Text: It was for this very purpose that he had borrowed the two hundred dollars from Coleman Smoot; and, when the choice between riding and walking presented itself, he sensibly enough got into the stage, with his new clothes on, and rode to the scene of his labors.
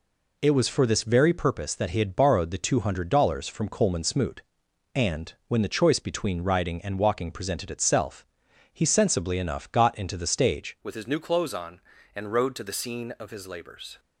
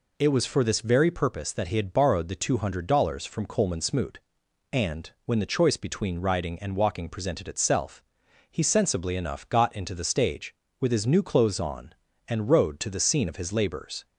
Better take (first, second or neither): second